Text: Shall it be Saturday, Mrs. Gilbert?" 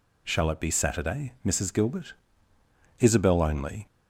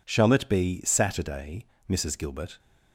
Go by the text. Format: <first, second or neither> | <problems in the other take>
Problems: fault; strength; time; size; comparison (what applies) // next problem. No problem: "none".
second | goes on to say "Isabel only"; noticeable; from 3.0 s on; 0.86 s long